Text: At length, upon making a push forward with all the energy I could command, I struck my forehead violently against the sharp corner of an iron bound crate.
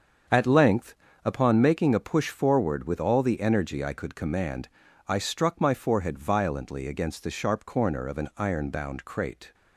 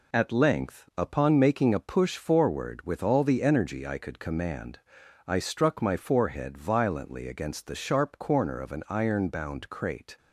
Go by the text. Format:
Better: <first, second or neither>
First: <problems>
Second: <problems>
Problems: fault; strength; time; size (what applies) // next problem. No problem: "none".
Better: second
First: starts louder than the rest; until 1.5 s; 7 dB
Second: none